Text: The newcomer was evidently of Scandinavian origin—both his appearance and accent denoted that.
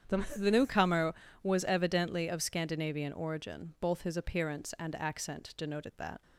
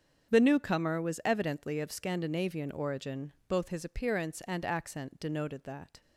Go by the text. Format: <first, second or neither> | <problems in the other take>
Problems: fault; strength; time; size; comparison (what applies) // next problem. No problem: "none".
second | starts louder than the rest; strong; until 1.5 s; 8.5 dB; strong in the second // says "The" twice; at 0.3 s